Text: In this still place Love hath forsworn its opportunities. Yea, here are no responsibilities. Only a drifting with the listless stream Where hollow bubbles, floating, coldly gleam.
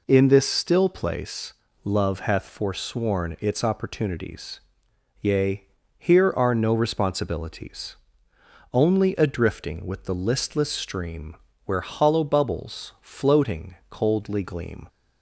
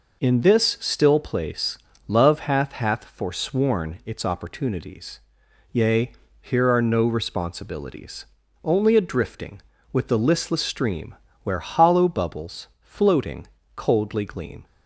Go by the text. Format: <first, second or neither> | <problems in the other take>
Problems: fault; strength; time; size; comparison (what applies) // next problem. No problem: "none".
first | pauses between "place" and "Love"; slight; at 1.7 s; 0.30 s long; slight in the first // says "hath" twice; at 2.7 s // pauses between "stream" and "Where"; slight; at 11.1 s; 0.28 s long; slight in the first